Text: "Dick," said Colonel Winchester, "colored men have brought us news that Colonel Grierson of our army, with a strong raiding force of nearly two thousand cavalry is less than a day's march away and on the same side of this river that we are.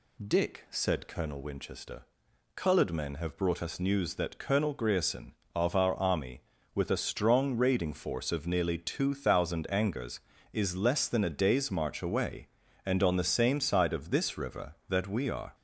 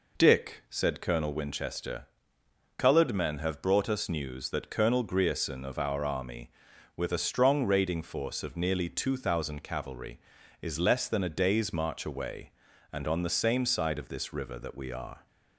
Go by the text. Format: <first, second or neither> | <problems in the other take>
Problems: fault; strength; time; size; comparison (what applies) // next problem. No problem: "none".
second | says "angers" for "cavalry"; at 9.6 s